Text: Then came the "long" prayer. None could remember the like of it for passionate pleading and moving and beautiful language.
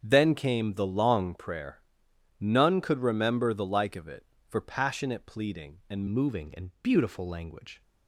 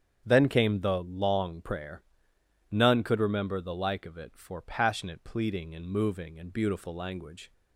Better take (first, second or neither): second